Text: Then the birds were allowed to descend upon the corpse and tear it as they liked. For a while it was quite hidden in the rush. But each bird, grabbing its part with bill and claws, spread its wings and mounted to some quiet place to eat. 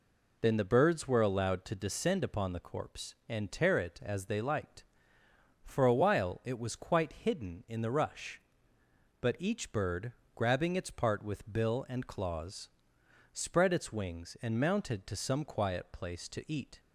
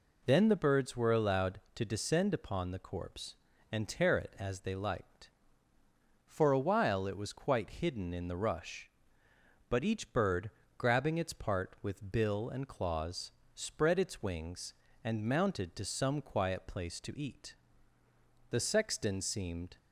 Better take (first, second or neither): first